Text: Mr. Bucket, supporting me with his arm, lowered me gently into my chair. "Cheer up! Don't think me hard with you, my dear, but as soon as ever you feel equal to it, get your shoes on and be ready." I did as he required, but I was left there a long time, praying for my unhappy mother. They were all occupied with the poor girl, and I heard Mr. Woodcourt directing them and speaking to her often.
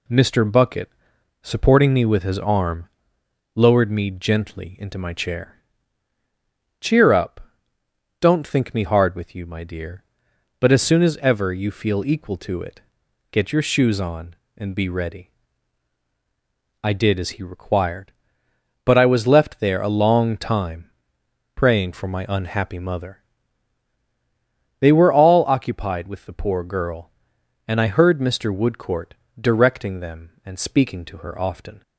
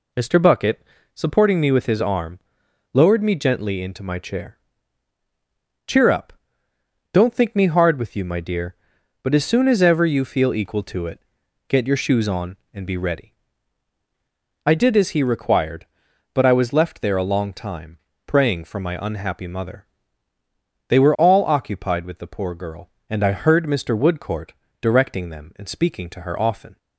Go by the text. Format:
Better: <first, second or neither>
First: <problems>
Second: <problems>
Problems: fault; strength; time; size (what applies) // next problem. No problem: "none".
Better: neither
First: pauses between "Woodcourt" and "directing"; slight; at 29.1 s; 0.26 s long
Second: pauses between "Woodcourt" and "directing"; slight; at 24.5 s; 0.26 s long